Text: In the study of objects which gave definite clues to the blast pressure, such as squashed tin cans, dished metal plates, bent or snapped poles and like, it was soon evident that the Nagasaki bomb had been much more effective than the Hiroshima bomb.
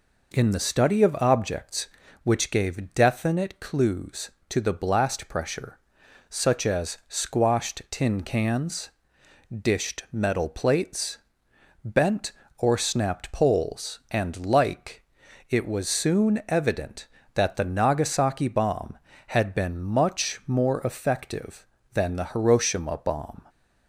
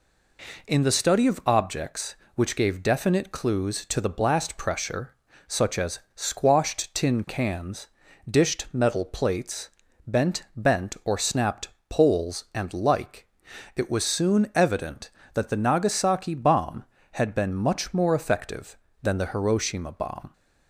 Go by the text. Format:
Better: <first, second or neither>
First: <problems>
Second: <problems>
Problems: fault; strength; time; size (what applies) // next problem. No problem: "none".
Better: first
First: none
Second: pauses between "as" and "squashed"; slight; at 5.9 s; 0.16 s long // says "bent" twice; at 10.5 s // pauses between "snapped" and "poles"; slight; at 11.6 s; 0.20 s long